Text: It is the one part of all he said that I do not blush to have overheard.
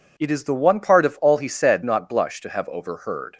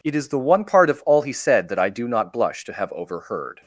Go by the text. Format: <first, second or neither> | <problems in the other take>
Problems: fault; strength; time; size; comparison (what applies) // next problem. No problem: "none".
second | skips "that I do"; at 1.8 s